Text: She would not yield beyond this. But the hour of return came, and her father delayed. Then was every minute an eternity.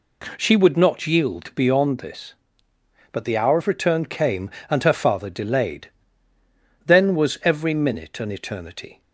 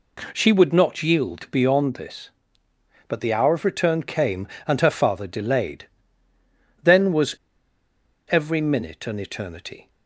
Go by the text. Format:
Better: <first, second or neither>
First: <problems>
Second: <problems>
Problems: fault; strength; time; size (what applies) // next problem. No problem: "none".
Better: first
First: none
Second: pauses between "was" and "every"; noticeable; at 7.3 s; 0.95 s long